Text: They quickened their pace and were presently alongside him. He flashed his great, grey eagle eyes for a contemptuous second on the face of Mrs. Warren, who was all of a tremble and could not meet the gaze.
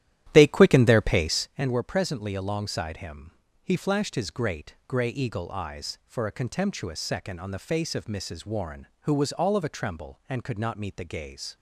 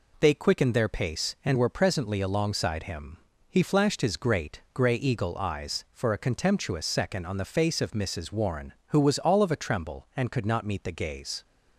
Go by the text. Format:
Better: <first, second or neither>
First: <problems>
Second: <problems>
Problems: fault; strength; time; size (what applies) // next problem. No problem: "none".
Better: second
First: starts louder than the rest; strong; until 1.5 s; 12.5 dB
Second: none